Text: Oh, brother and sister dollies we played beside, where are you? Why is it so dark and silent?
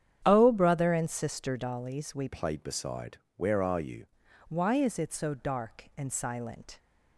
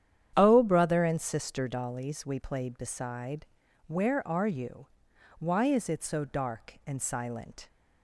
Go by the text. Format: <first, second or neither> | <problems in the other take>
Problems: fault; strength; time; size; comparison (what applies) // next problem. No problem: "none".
second | starts louder than the rest; strong; until 1.2 s; 9 dB; strong in the second // changes voice from "played" to "you"; from 2.2 to 4.0 s; 1.8 s long